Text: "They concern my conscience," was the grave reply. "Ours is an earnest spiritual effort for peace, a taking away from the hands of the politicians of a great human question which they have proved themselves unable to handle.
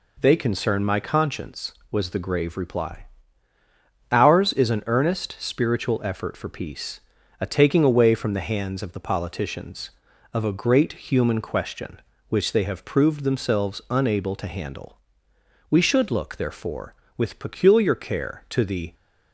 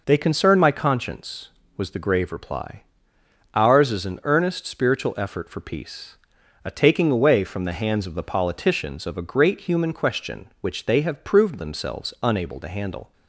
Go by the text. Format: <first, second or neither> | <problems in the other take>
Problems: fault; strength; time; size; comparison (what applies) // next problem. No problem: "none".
second | goes on to say "We should look therefore with peculiar care to the"; strong; from 15.6 s on; 3.2 s long